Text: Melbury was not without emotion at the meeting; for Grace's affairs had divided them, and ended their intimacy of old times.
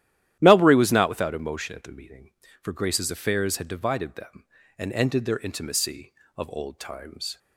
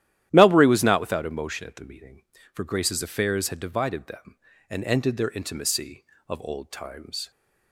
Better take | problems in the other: neither | starts louder than the rest; strong; the same in both

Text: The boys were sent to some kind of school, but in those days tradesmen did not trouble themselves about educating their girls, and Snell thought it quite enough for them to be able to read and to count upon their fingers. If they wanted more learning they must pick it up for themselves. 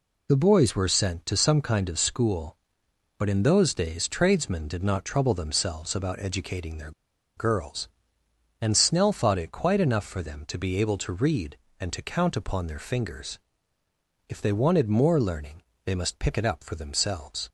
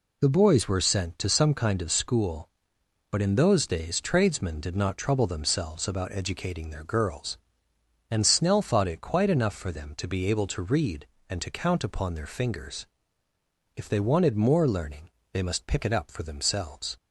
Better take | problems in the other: second | pauses between "their" and "girls"; at 6.9 s; 0.45 s long // pauses between "learning" and "they"; slight; at 15.6 s; 0.22 s long; slight in the second

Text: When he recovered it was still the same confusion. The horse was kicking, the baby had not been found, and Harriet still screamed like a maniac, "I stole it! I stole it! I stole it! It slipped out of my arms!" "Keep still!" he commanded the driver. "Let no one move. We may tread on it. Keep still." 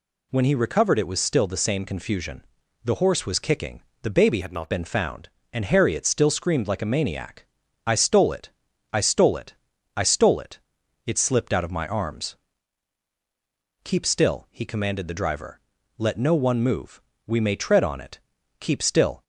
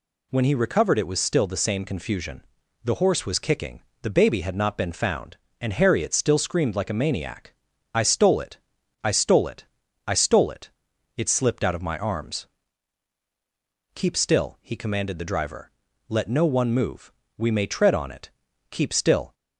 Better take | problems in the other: second | changes voice from "had" to "not"; from 4.4 to 4.6 s; 0.2 s long

